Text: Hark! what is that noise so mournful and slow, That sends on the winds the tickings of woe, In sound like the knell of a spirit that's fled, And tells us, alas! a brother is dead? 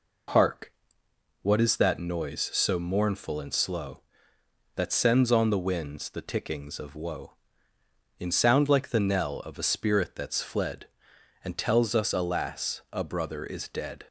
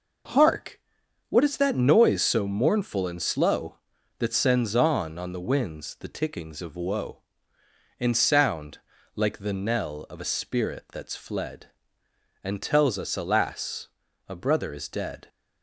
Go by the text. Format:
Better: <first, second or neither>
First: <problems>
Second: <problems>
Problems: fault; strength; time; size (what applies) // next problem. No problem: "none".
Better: first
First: none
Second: says "on" twice; at 5.1 s // pauses between "sound" and "like"; slight; at 8.7 s; 0.36 s long